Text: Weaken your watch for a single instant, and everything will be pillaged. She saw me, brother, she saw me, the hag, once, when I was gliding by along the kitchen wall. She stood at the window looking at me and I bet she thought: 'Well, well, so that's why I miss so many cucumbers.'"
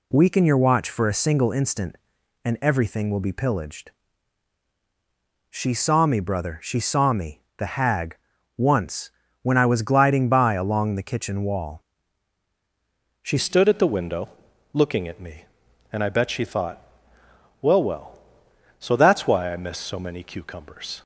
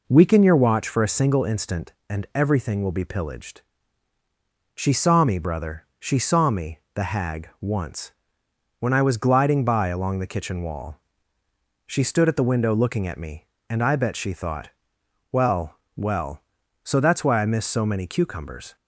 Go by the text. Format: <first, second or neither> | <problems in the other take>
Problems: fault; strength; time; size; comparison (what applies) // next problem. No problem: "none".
second | changes voice at "stood"; from 13.3 s on; 7.7 s long // pauses between "window" and "looking"; noticeable; at 14.2 s; 0.46 s long